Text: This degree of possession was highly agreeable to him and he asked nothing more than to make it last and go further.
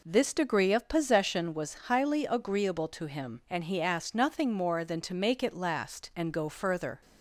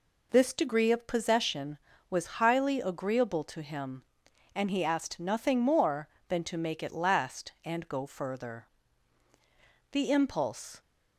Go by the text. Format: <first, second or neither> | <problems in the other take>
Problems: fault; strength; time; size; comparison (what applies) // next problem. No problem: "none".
first | goes on to say "The impulse"; noticeable; from 9.9 s on; 0.88 s long